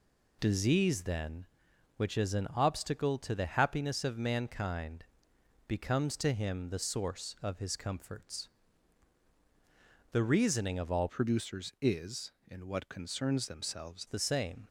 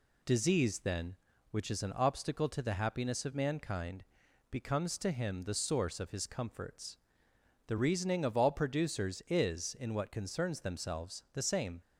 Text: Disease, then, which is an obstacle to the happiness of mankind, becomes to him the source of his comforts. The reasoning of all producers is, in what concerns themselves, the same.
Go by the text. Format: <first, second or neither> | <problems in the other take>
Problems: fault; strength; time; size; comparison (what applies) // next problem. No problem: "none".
second | changes voice from "producers" to "themselves"; from 11.0 to 14.0 s; 3.0 s long